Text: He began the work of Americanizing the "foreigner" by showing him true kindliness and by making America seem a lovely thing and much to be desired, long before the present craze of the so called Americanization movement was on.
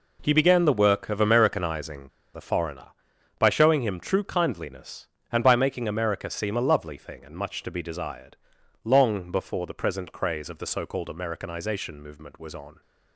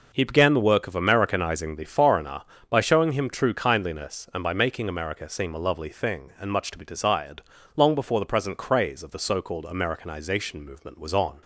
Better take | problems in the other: second | pauses between "Americanizing" and "the"; slight; at 2.0 s; 0.25 s long

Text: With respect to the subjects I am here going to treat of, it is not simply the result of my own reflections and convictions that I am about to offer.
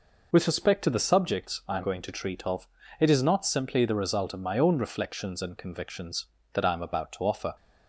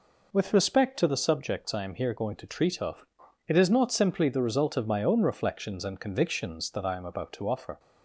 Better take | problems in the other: second | skips "here"; at 1.8 s

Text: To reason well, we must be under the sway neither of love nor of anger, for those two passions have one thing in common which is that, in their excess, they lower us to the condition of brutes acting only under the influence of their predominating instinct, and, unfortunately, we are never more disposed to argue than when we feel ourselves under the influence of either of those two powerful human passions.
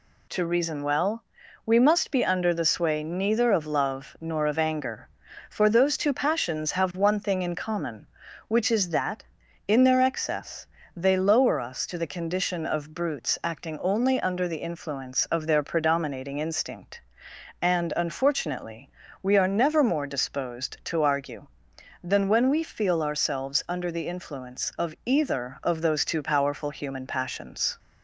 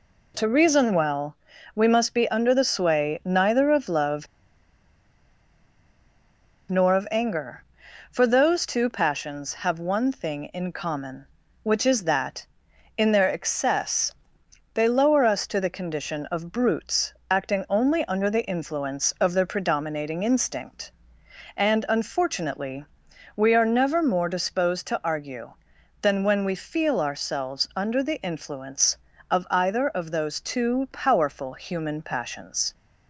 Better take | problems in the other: first | pauses between "love" and "nor"; strong; at 4.2 s; 2.4 s long // pauses between "brutes" and "acting"; slight; at 17.1 s; 0.18 s long

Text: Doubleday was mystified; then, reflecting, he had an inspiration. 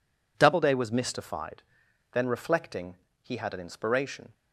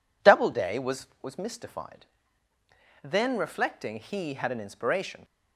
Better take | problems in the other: first | says "was" twice; at 1.2 s

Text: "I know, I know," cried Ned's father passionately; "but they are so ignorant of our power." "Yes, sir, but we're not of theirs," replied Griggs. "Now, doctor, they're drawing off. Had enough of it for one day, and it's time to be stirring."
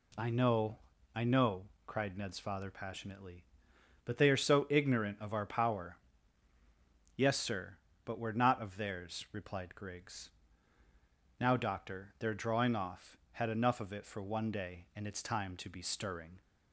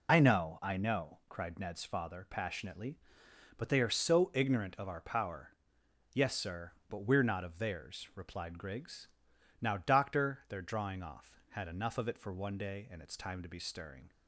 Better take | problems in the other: first | loses the start of "I"; at 0.0 s; 50 ms

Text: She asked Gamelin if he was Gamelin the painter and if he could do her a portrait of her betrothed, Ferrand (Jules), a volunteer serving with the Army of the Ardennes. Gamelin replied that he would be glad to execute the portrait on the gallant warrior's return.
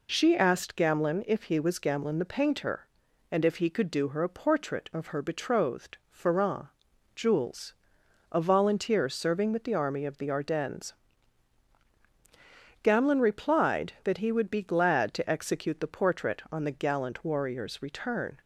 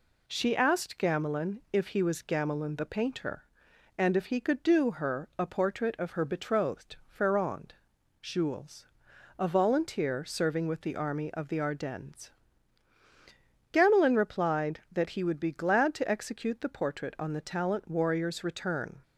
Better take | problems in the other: first | says "talent" for "gallant"; at 17.4 s

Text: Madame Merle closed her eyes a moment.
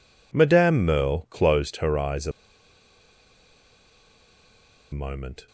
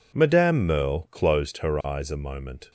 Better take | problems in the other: second | pauses between "a" and "moment"; strong; at 2.3 s; 2.6 s long

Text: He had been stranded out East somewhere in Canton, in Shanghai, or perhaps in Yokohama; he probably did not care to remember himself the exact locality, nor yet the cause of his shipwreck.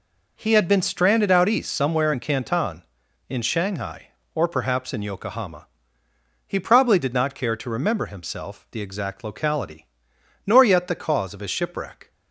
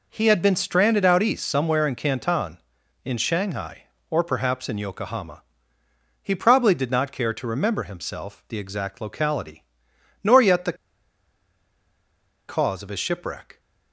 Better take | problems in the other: first | pauses between "the" and "cause"; strong; at 10.7 s; 1.7 s long

